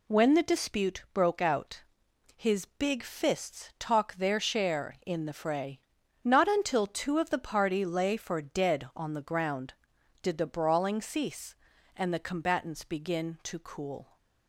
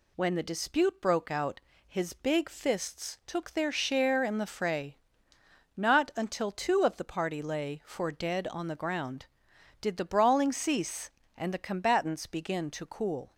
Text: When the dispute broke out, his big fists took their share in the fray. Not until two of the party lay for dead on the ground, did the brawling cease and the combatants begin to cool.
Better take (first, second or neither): second